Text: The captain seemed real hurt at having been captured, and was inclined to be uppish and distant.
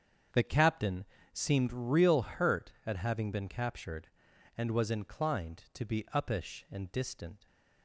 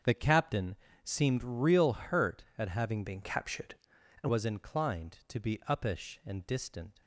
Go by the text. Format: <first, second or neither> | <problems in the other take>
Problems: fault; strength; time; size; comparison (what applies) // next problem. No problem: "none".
first | starts louder than the rest; strong; until 1.3 s; 7 dB; strong in the first // pauses between "captain" and "seemed"; slight; at 0.7 s; 0.30 s long; slight in the first // changes voice from "been" to "and"; from 3.0 to 4.2 s; 1.2 s long